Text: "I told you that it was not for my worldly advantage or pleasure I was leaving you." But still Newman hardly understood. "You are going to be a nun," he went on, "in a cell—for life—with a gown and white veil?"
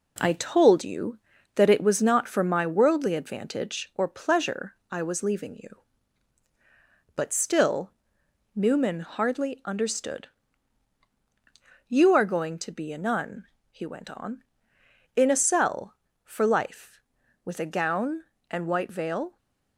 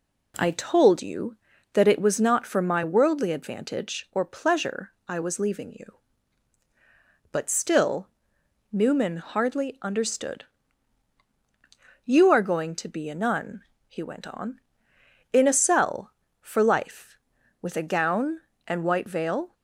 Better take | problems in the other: second | gets quieter; noticeable; throughout; 4 dB // pauses between "pleasure" and "I"; slight; at 4.7 s; 0.16 s long; slight in the second // pauses between "still" and "Newman"; noticeable; at 7.9 s; 0.64 s long; noticeable in the second

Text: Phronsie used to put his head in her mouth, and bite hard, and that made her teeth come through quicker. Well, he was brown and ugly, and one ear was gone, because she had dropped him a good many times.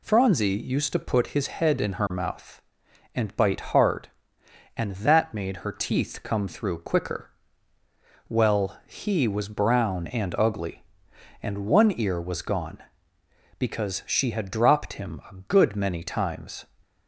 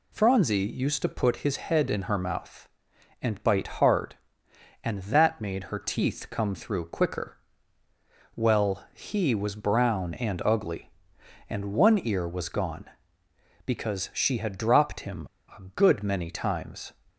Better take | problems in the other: first | pauses between "bite" and "hard"; slight; at 3.6 s; 0.16 s long; slight in the first // pauses between "him" and "a"; slight; at 15.2 s; 0.28 s long

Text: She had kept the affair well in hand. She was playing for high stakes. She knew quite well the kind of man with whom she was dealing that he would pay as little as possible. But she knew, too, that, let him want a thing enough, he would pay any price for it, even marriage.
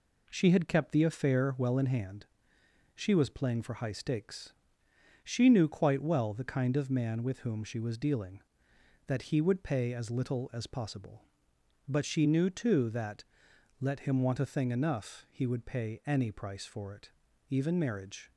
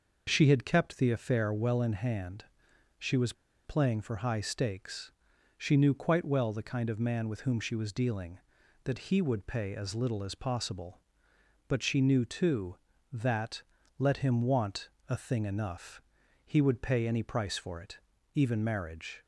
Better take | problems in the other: first | pauses between "was" and "playing"; slight; at 3.3 s; 0.32 s long // pauses between "want" and "a"; slight; at 14.8 s; 0.18 s long

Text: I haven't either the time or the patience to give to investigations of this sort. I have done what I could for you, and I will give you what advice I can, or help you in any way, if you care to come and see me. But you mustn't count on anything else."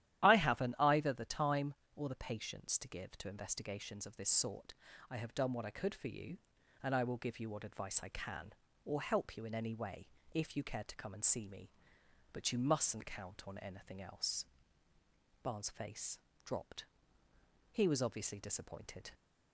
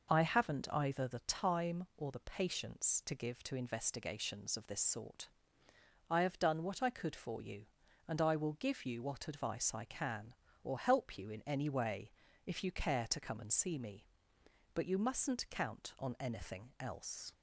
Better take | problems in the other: second | starts louder than the rest; strong; until 1.2 s; 12 dB // goes on to say "Barnes face dropped He was obviously disappointed"; strong; from 15.4 s on; 3.7 s long

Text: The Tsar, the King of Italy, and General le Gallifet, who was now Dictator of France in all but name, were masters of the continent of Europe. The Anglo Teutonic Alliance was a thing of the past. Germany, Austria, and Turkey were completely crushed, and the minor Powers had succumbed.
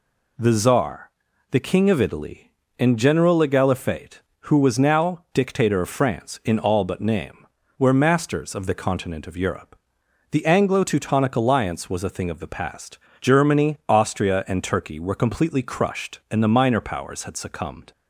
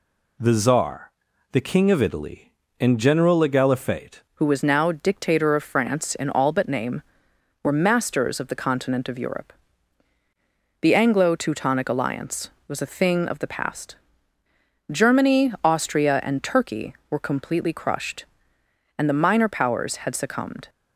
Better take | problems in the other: first | changes voice at "who"; from 4.3 s on; 16.3 s long

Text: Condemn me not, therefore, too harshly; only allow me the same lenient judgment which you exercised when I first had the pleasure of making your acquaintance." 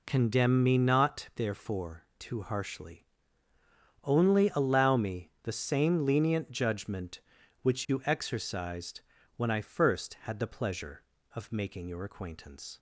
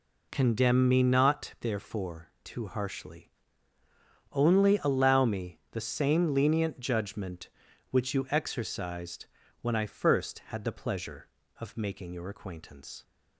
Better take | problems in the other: neither | pauses between "exercised" and "when"; slight; the same in both

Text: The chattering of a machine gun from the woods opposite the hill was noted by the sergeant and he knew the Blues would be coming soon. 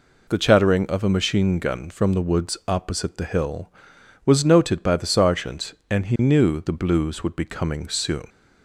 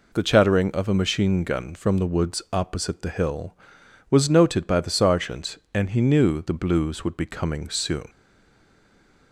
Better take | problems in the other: first | stays silent after the last word; noticeable; from 8.0 s on; 1.3 s long

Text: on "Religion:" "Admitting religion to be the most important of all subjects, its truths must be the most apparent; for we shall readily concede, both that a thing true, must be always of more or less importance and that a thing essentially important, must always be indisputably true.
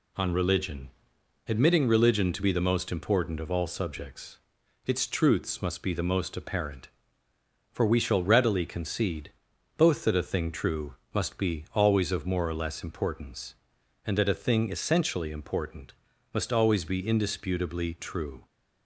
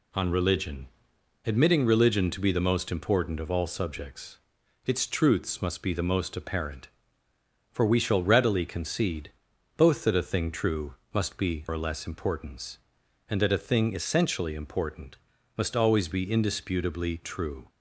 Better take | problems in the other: first | skips "always of more"; at 11.6 s

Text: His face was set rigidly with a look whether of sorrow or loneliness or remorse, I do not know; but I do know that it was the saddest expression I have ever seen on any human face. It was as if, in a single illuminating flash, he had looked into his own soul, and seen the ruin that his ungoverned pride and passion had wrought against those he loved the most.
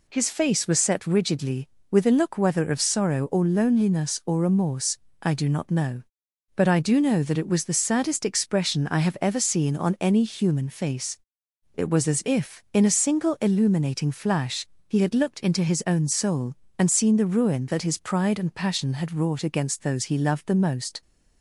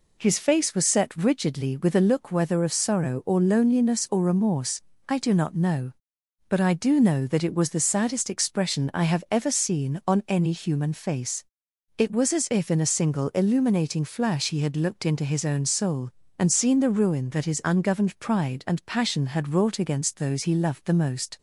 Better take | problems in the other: second | skips "ungoverned"; at 17.9 s

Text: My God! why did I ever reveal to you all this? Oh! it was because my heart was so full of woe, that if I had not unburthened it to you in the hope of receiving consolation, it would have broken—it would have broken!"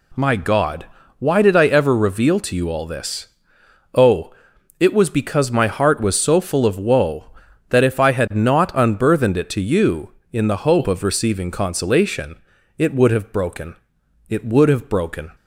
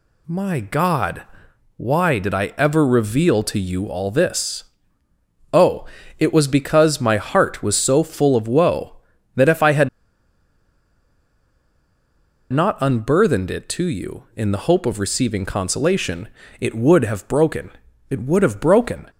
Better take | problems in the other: first | pauses between "had" and "not"; strong; at 9.8 s; 2.6 s long

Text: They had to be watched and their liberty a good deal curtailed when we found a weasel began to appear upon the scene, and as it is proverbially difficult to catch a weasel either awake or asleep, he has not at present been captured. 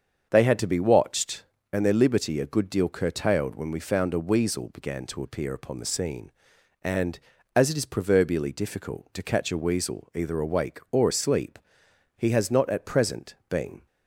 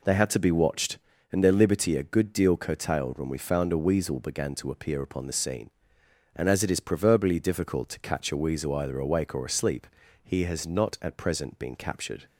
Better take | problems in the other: second | starts louder than the rest; until 1.3 s; 7 dB // stops before "captured"; at 13.8 s

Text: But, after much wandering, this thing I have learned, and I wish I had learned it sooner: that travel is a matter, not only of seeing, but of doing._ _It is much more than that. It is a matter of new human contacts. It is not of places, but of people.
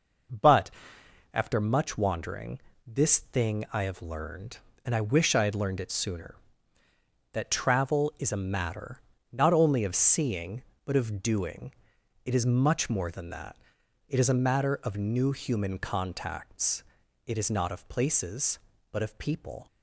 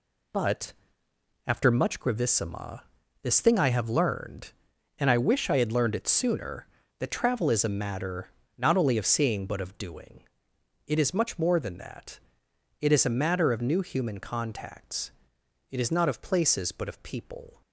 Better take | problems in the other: first | says "gravissima" for "wandering"; at 1.9 s

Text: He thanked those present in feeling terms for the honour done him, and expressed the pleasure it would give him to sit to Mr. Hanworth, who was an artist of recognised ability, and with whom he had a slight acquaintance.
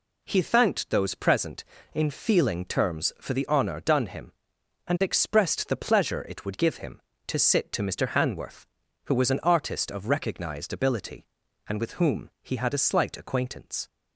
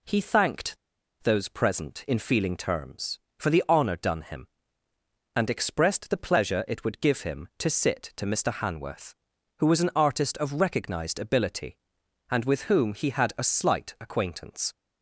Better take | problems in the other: first | pauses between "thanked" and "those"; noticeable; at 0.7 s; 0.48 s long

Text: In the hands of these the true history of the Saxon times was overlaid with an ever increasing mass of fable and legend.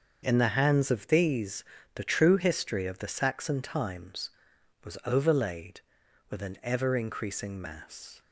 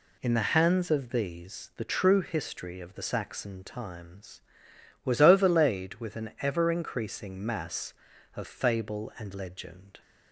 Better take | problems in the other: second | starts louder than the rest; until 1.2 s; 6.5 dB // pauses between "these" and "the"; slight; at 1.6 s; 0.32 s long // stops before "of fable and legend"; at 8.2 s

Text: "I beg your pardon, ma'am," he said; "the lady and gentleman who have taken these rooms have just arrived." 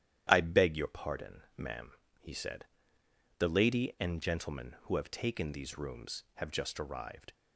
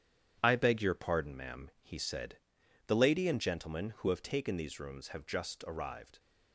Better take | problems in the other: first | gets quieter; strong; throughout; 7.5 dB // starts louder than the rest; strong; until 1.4 s; 10 dB; strong in the first

